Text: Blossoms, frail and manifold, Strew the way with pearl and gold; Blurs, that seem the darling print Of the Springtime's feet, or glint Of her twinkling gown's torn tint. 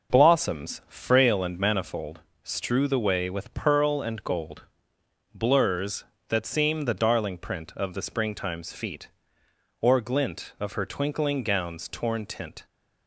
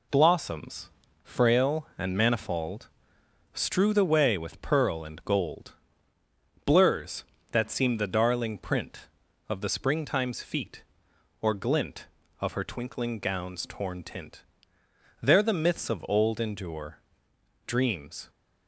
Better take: first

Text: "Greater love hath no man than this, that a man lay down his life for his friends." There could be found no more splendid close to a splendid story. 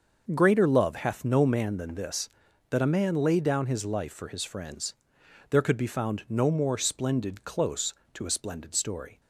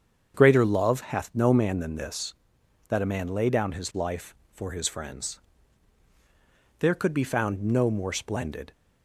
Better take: first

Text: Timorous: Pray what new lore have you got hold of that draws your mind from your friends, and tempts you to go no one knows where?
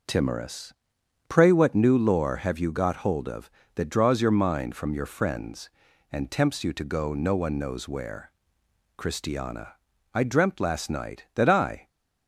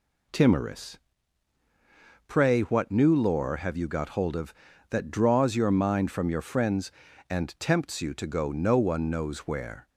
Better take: second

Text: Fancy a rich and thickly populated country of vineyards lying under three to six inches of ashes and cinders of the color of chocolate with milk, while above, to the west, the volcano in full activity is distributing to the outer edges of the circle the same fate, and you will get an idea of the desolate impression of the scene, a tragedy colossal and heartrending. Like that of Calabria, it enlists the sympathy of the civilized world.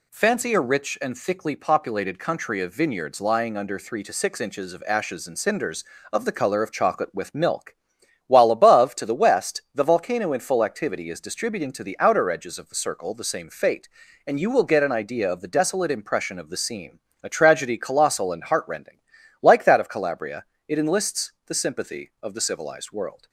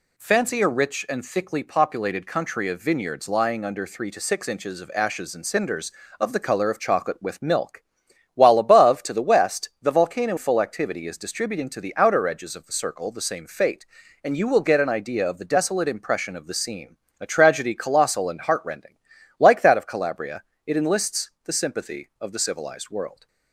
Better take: first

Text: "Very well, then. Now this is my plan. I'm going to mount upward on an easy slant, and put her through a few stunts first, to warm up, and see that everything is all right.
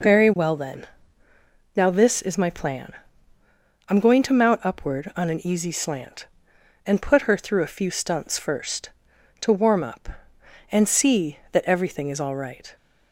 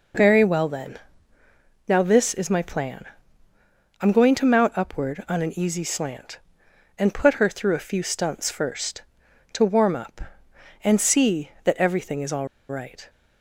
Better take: first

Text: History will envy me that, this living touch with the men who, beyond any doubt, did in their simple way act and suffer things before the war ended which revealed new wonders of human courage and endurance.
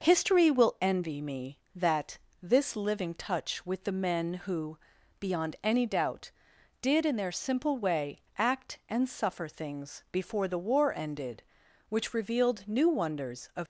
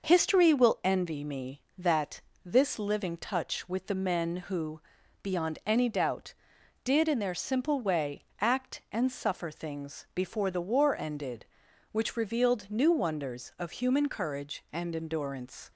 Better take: second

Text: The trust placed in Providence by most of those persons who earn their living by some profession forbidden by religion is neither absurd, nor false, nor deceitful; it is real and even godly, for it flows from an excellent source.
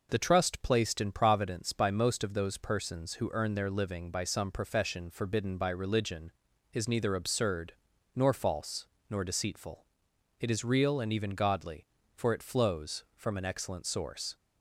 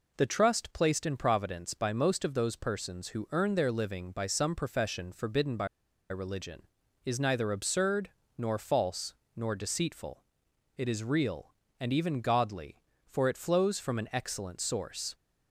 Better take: first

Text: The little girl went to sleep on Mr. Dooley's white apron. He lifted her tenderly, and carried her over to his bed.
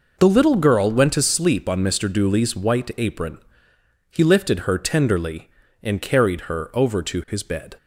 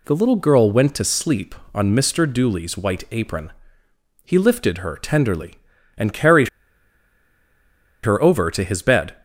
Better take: first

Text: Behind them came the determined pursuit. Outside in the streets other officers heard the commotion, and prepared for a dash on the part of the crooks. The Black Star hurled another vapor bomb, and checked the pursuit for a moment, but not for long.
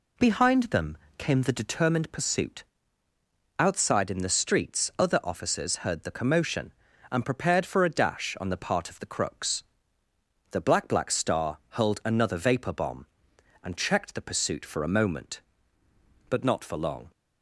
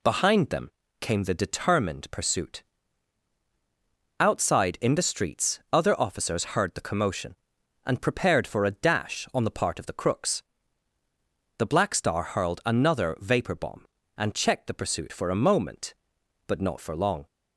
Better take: second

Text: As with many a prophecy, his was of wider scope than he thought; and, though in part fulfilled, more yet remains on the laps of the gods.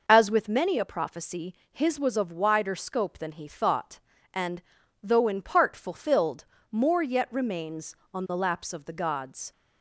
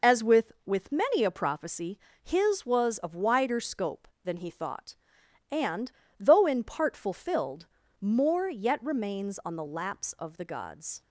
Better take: first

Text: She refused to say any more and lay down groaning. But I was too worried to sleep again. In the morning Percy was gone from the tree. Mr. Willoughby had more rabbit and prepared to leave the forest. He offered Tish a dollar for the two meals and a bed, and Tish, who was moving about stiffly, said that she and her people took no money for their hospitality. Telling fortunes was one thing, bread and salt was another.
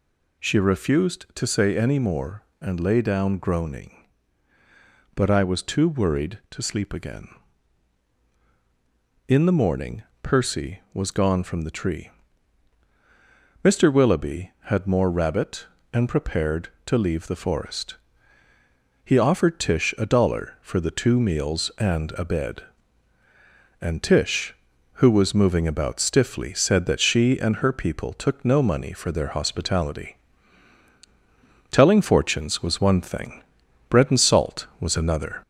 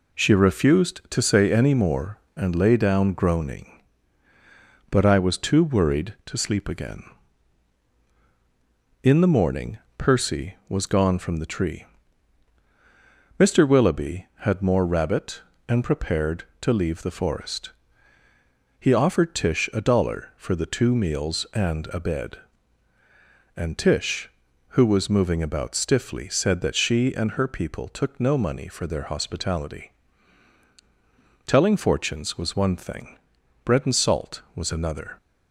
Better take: second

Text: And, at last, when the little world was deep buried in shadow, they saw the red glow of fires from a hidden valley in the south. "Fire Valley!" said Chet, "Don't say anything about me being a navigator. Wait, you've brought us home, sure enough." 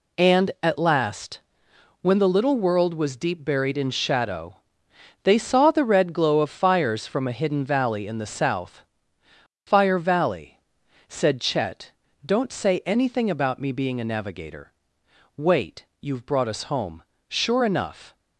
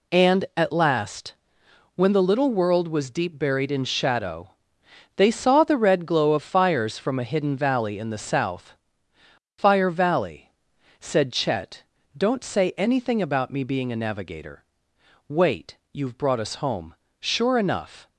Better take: neither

